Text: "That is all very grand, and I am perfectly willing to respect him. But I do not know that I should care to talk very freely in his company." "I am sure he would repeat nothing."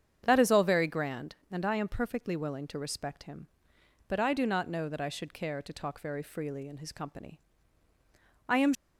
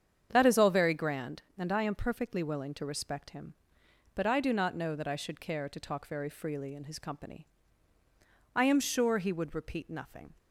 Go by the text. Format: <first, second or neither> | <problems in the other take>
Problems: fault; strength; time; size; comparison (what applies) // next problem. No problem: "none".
second | starts louder than the rest; strong; until 1.2 s; 8 dB; strong in the second // stops before "sure he would repeat nothing"; at 8.7 s